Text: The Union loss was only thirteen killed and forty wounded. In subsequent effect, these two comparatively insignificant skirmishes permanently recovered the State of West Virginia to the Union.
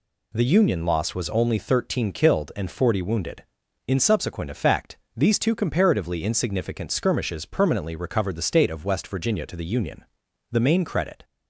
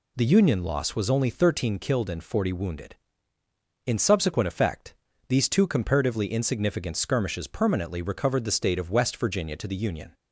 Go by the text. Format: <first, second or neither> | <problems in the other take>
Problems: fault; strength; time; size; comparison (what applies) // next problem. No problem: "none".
second | goes on to say "The main credit"; noticeable; from 10.4 s on; 0.74 s long